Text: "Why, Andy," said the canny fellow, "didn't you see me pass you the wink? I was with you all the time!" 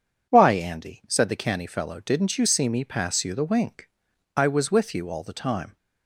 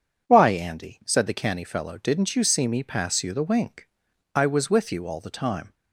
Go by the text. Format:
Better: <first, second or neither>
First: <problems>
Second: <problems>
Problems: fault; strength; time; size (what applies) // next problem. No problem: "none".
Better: neither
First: none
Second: none